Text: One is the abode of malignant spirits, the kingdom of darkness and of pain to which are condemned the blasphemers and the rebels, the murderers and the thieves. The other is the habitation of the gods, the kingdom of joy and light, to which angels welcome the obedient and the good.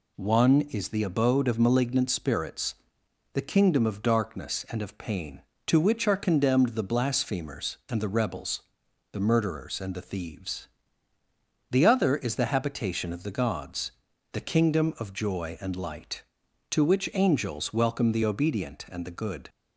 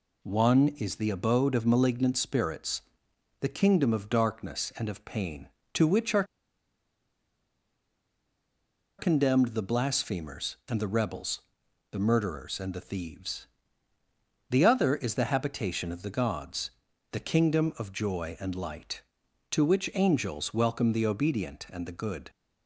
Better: first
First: none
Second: pauses between "are" and "condemned"; strong; at 6.2 s; 2.7 s long

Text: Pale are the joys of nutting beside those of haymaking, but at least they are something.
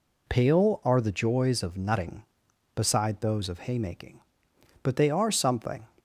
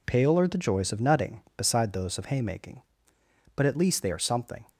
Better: second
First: skips "at least"; at 4.9 s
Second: none

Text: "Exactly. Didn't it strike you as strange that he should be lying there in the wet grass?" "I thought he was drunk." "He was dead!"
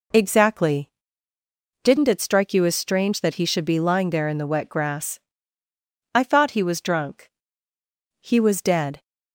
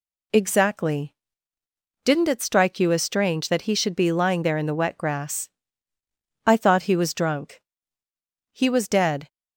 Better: neither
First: none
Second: none

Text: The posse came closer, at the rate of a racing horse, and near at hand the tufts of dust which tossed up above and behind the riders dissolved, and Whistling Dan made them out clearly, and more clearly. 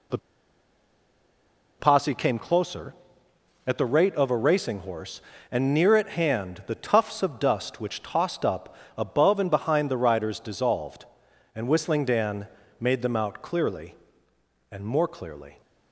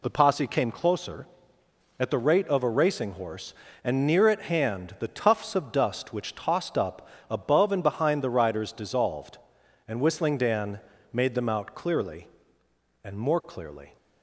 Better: second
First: pauses between "The" and "posse"; strong; at 0.1 s; 1.6 s long // pauses between "up" and "above"; slight; at 8.7 s; 0.22 s long // pauses between "Dan" and "made"; slight; at 12.4 s; 0.34 s long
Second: pauses between "up" and "above"; slight; at 7.0 s; 0.22 s long // pauses between "Dan" and "made"; slight; at 10.7 s; 0.34 s long

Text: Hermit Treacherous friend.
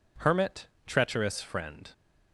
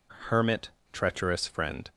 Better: neither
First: pauses between "Hermit" and "Treacherous"; slight; at 0.6 s; 0.20 s long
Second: pauses between "Hermit" and "Treacherous"; slight; at 0.6 s; 0.22 s long

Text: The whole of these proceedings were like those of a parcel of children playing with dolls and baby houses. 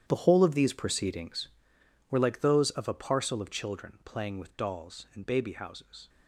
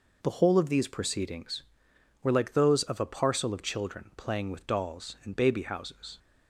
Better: second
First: gets quieter; strong; throughout; 14.5 dB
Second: none

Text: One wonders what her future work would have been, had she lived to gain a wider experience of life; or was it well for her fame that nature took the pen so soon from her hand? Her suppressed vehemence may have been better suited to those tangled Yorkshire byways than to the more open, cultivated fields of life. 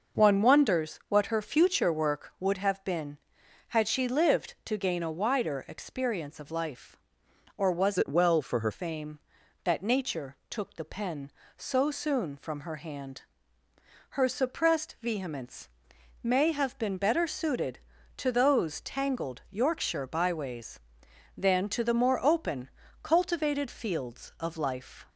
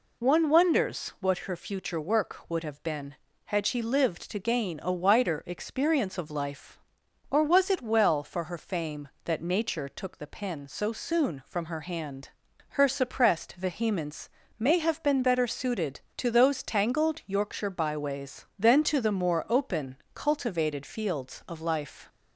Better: second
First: changes voice from "it" to "her"; from 7.9 to 8.7 s; 0.8 s long // pauses between "vehemence" and "may"; noticeable; at 15.6 s; 0.56 s long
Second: pauses between "vehemence" and "may"; slight; at 14.2 s; 0.28 s long

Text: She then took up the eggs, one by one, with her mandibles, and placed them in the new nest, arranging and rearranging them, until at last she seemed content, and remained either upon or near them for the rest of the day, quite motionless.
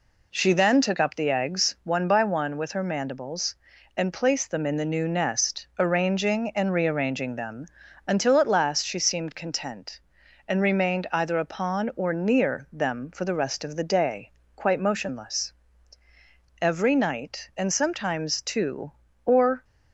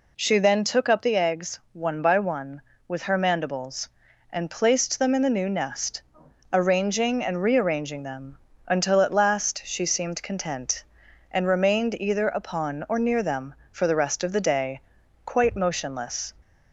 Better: second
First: goes on to say "Every night and sometimes two or"; strong; from 16.6 s on; 3.0 s long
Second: none

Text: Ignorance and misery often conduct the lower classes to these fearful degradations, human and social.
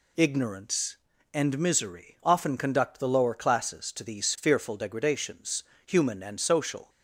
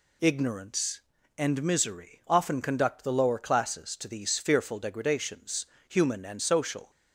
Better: neither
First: none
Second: none

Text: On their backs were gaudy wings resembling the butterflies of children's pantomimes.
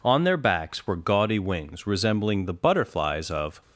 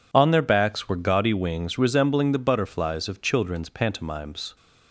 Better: second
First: stops before "children's pantomimes"; at 3.6 s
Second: none

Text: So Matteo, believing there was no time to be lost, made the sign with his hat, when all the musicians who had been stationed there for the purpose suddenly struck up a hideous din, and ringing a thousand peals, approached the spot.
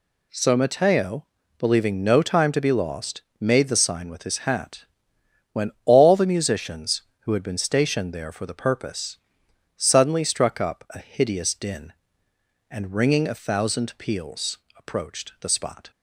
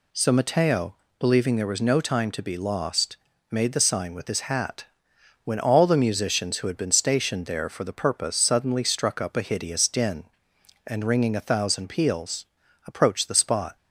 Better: second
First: skips "there was"; at 2.0 s // pauses between "purpose" and "suddenly"; noticeable; at 9.1 s; 0.60 s long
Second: none

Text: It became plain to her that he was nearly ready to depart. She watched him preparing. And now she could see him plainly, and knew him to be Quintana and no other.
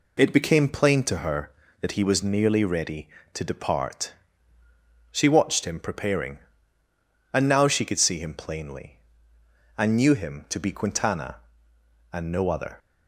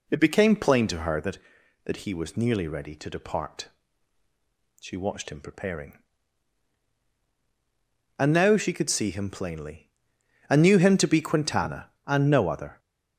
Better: first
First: none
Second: says "that" twice; at 1.8 s

